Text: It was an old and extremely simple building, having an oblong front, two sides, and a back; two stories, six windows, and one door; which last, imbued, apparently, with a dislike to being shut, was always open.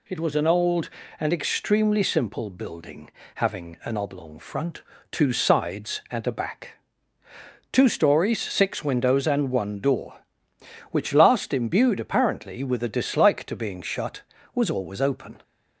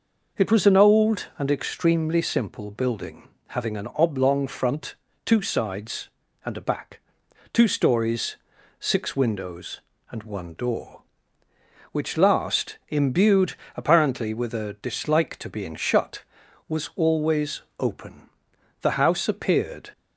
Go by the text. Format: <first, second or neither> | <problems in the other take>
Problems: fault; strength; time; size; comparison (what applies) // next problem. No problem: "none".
first | pauses between "always" and "open"; slight; at 17.6 s; 0.16 s long // goes on to say "The house appeared"; noticeable; from 18.8 s on; 1.1 s long